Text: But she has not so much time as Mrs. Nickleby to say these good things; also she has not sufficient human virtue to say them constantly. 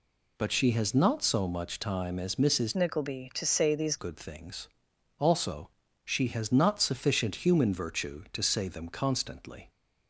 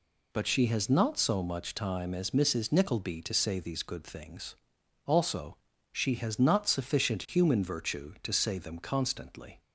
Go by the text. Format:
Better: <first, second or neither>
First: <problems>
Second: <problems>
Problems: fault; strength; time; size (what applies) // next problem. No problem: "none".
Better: second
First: changes voice from "Nickleby" to "these"; from 2.7 to 3.9 s; 1.2 s long // pauses between "also" and "she"; slight; at 5.6 s; 0.34 s long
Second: pauses between "also" and "she"; slight; at 5.5 s; 0.34 s long